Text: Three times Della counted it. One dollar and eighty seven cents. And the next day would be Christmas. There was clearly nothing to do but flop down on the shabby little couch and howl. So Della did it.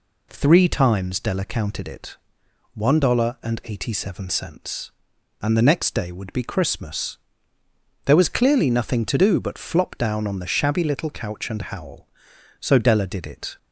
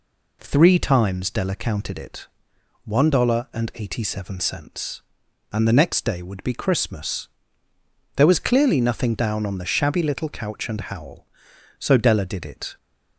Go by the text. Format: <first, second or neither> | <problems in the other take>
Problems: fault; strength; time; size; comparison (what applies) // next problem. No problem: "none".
first | skips "to do but flop"; at 9.1 s